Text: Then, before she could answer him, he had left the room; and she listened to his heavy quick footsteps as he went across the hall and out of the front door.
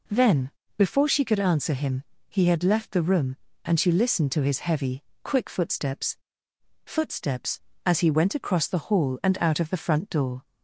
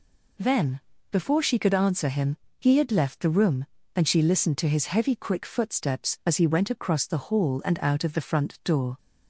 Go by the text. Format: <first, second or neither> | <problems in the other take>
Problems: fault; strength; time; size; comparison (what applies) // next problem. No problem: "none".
second | pauses between "heavy" and "quick"; slight; at 5.0 s; 0.20 s long // says "footsteps" twice; at 6.8 s